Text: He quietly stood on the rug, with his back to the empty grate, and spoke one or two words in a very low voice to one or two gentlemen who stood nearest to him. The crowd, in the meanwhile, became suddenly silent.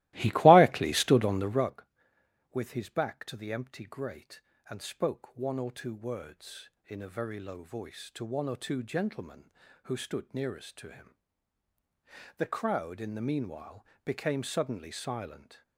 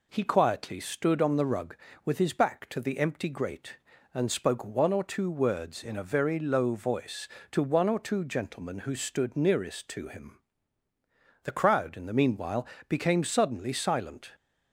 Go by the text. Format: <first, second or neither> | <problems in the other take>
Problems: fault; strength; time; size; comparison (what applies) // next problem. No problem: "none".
second | starts louder than the rest; strong; until 1.7 s; 18 dB